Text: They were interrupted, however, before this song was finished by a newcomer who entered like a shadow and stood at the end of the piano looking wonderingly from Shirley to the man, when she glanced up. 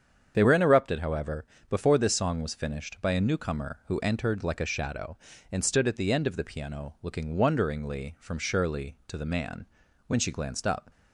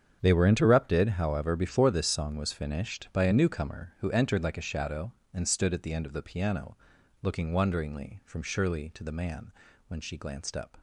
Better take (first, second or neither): first